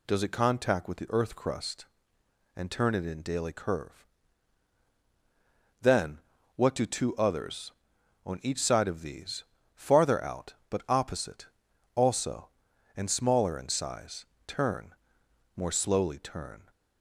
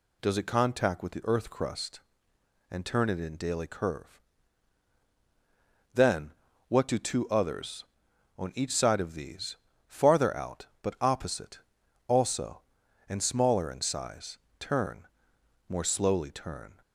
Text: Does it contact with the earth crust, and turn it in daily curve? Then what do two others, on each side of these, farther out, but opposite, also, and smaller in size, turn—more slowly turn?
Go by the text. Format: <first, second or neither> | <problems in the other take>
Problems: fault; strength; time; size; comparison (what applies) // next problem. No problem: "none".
neither | pauses between "Then" and "what"; slight; the same in both